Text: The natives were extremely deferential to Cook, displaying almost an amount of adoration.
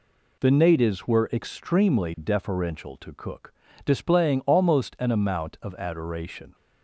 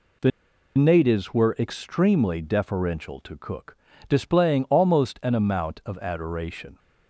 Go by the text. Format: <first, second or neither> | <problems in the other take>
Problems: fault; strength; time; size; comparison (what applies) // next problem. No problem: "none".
first | pauses between "The" and "natives"; noticeable; at 0.3 s; 0.48 s long